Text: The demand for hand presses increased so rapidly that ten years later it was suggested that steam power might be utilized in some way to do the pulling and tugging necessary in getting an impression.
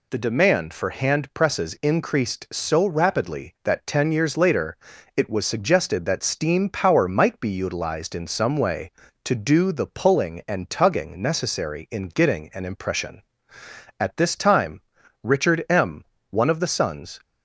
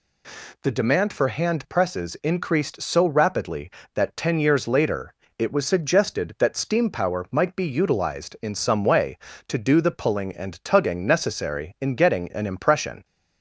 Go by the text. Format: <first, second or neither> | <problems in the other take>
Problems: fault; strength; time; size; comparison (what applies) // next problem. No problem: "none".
second | pauses between "later" and "it"; at 4.7 s; 0.38 s long; slight in the second // goes on to say "At this time Richard M one of the sons"; strong; from 13.9 s on; 3.2 s long